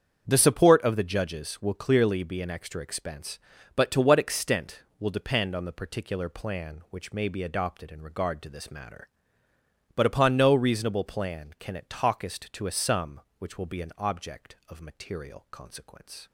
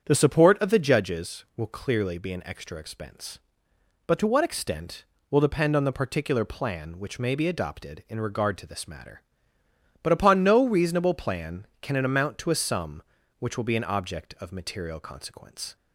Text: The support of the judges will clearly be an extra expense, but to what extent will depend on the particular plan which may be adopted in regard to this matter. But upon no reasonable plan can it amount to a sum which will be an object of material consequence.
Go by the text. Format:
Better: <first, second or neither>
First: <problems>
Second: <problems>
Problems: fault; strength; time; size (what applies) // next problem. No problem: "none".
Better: second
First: starts louder than the rest; strong; until 1.2 s; 7.5 dB // says "talkest" for "amount"; at 11.8 s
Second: starts louder than the rest; strong; until 1.0 s; 8 dB